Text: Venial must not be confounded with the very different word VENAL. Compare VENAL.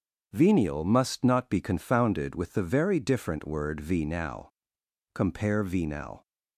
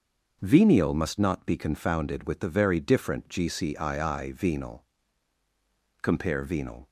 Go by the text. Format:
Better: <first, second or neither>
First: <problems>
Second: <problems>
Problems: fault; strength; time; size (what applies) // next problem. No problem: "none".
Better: first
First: starts louder than the rest; strong; until 1.3 s; 7.5 dB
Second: starts louder than the rest; noticeable; until 1.4 s; 6 dB // says "gcii" for "word"; at 3.2 s